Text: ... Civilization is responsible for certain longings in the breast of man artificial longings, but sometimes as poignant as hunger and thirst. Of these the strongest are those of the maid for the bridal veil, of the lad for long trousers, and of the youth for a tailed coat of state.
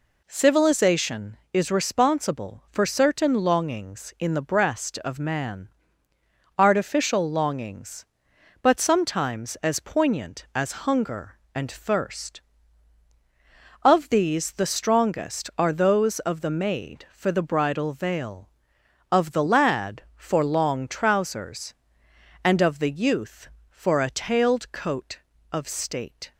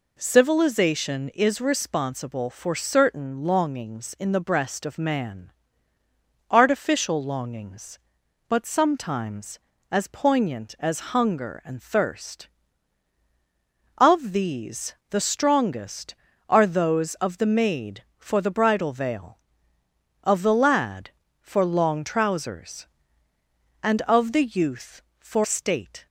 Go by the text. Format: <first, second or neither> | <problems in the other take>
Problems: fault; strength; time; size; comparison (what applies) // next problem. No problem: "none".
first | pauses between "man" and "artificial"; noticeable; at 5.5 s; 0.98 s long; noticeable in the first // skips "a tailed coat of"; at 25.4 s